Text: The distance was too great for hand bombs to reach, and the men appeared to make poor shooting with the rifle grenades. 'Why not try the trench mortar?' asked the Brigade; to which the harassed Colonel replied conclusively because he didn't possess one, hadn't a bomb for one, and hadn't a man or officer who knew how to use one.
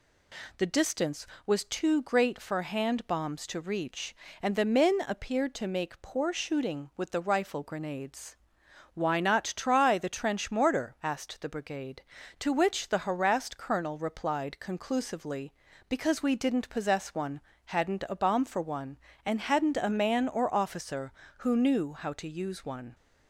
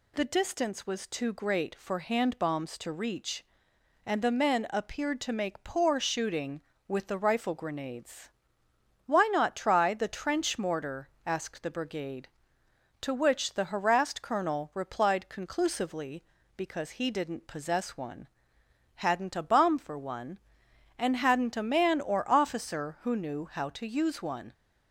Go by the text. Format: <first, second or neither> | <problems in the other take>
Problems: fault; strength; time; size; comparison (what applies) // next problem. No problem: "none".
second | says "we" for "he"; at 16.2 s